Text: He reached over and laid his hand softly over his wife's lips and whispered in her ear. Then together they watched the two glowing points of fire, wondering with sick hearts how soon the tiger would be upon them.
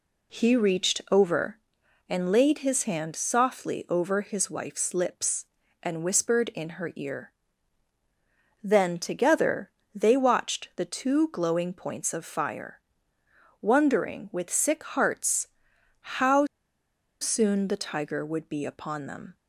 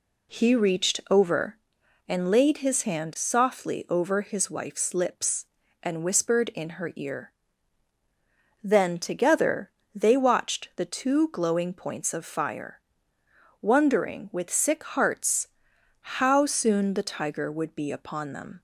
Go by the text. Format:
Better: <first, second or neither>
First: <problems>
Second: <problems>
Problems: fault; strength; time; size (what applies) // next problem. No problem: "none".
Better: second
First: pauses between "together" and "they"; slight; at 9.7 s; 0.22 s long // pauses between "hearts" and "how"; noticeable; at 15.4 s; 0.50 s long // pauses between "how" and "soon"; noticeable; at 16.4 s; 0.76 s long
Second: pauses between "together" and "they"; slight; at 9.7 s; 0.22 s long // pauses between "hearts" and "how"; noticeable; at 15.4 s; 0.50 s long